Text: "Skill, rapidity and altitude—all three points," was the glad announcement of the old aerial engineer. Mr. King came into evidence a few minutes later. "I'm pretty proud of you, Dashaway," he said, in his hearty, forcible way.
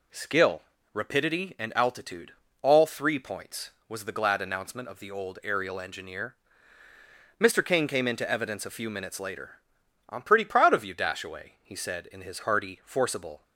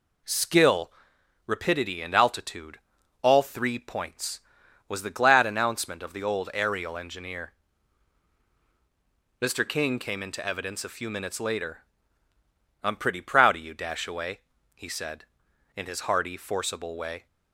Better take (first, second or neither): second